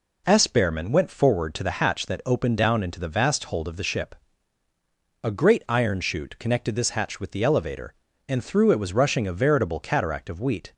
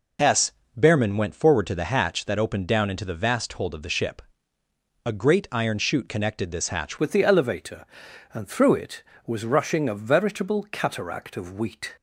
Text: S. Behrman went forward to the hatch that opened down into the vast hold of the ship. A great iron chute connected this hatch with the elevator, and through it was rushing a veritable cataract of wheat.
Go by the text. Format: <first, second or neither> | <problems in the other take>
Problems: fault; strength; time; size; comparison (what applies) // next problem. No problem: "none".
first | changes voice at "with"; from 6.9 s on; 5.0 s long